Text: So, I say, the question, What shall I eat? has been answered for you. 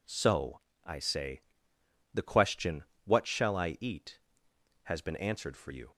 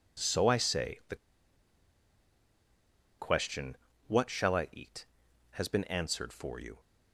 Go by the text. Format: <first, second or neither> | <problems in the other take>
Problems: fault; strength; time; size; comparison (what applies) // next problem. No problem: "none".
first | pauses between "the" and "question"; strong; at 1.1 s; 2.0 s long